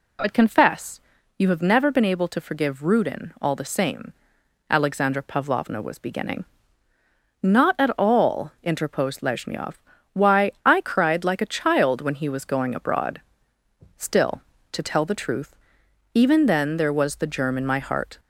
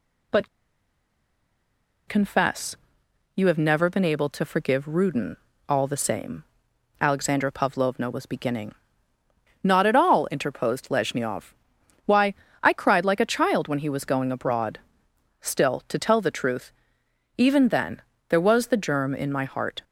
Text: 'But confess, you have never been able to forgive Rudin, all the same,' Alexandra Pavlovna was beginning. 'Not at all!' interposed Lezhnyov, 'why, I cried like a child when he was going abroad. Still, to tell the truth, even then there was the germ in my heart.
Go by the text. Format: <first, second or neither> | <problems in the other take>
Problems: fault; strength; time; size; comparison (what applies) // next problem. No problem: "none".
first | pauses between "But" and "confess"; strong; at 0.4 s; 1.5 s long // pauses between "then" and "there"; slight; at 18.0 s; 0.26 s long